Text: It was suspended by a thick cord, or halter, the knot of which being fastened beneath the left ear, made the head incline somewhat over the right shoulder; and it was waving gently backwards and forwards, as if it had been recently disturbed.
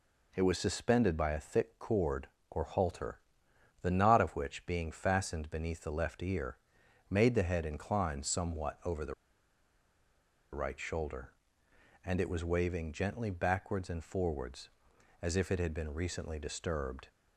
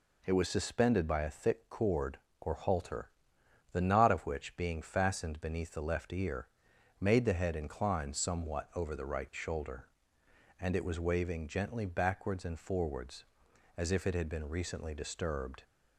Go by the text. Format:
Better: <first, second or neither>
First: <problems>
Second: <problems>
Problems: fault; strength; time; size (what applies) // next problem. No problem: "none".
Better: second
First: pauses between "the" and "right"; strong; at 9.1 s; 1.3 s long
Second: none